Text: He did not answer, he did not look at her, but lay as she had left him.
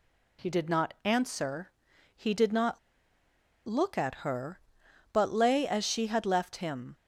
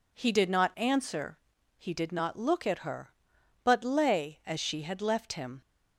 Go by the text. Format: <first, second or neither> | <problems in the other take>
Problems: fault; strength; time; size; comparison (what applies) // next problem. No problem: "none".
second | pauses between "not" and "look"; noticeable; at 2.7 s; 0.87 s long